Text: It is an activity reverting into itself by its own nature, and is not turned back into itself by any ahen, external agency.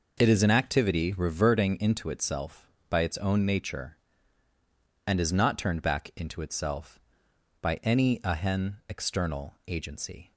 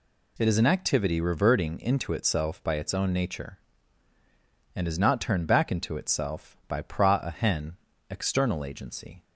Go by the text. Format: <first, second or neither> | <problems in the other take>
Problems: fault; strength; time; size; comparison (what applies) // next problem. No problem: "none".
first | says "pra" for "any"; at 6.8 s